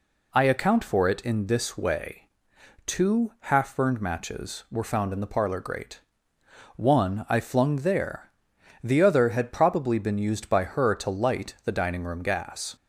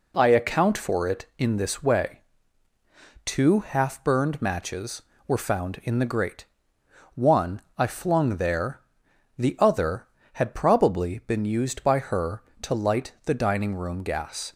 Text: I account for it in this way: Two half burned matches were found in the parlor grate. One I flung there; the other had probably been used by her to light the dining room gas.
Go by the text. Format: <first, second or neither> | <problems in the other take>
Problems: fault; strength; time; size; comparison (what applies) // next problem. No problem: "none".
first | skips "parlor"; at 6.0 s // pauses between "One" and "I"; slight; at 7.5 s; 0.18 s long